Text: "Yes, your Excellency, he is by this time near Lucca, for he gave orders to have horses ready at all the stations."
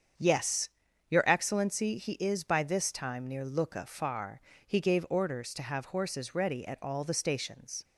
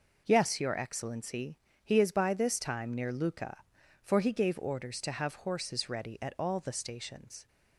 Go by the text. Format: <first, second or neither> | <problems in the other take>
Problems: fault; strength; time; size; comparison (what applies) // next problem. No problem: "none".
second | starts louder than the rest; strong; until 1.5 s; 7.5 dB // says "far" for "for"; at 3.8 s